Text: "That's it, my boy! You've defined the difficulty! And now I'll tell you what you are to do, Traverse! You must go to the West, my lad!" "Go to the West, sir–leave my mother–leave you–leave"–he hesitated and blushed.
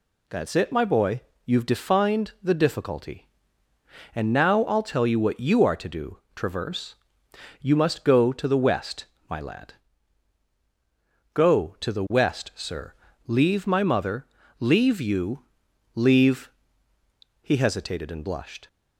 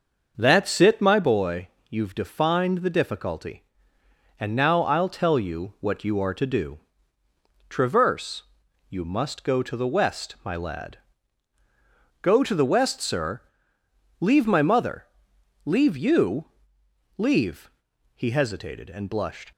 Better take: first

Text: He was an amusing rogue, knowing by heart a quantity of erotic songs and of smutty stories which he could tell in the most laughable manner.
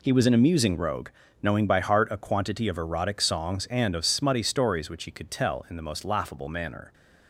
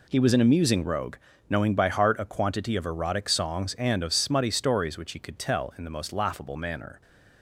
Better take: neither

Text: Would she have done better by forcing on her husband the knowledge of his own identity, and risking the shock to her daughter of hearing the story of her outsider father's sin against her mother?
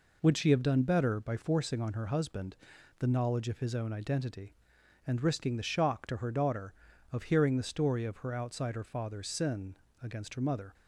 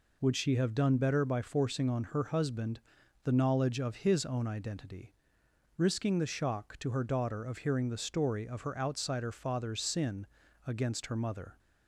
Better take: first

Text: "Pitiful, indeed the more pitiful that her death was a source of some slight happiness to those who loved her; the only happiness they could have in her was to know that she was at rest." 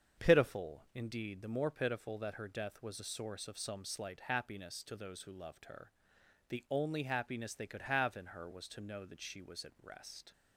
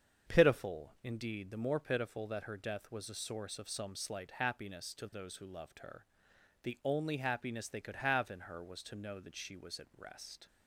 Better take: neither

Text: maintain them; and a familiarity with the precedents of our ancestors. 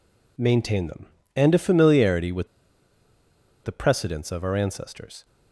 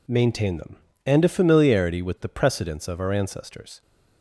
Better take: second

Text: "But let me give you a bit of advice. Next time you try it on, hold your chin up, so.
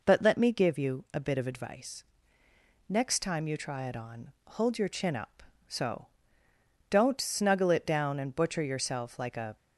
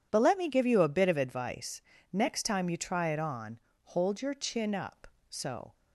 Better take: second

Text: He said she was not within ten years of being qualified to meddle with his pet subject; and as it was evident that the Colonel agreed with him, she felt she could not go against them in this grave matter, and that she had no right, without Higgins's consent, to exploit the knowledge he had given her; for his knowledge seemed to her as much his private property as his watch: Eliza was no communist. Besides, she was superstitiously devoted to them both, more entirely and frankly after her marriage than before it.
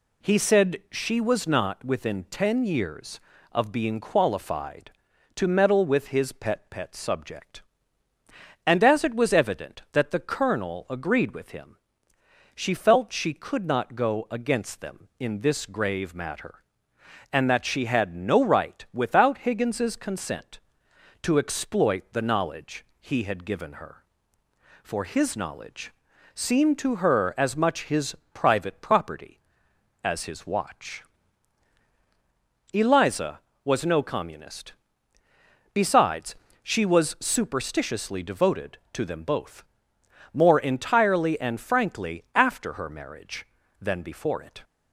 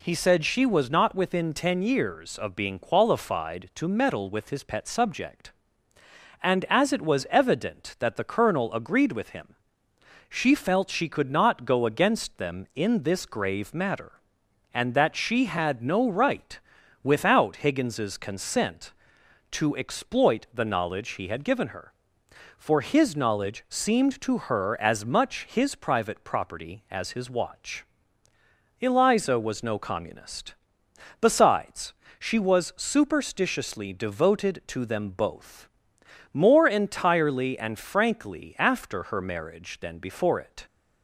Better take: second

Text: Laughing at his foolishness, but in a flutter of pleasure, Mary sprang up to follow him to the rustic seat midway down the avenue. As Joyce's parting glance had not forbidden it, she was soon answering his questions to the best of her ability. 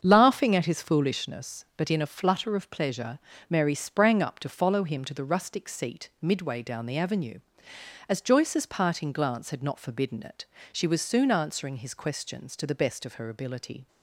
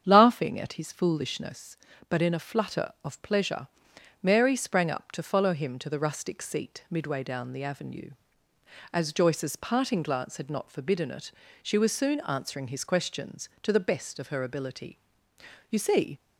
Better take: first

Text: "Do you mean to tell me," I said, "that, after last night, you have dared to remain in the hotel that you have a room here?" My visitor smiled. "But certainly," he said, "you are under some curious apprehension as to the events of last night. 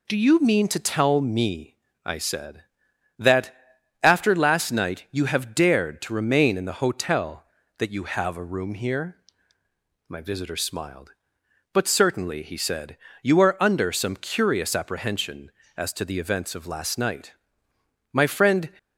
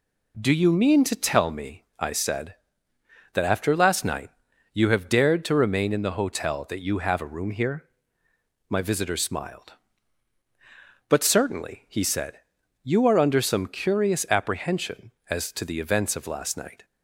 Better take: second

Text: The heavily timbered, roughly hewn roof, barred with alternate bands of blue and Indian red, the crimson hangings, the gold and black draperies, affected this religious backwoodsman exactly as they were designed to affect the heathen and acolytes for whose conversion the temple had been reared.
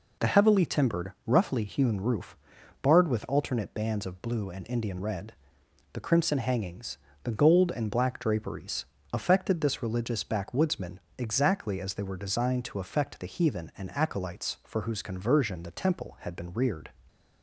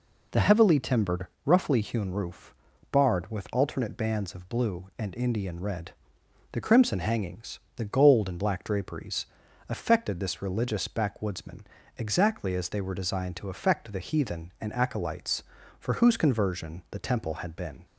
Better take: first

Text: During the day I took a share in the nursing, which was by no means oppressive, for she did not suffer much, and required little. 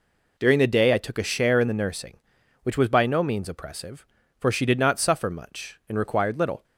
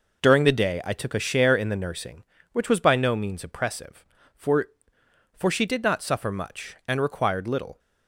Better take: first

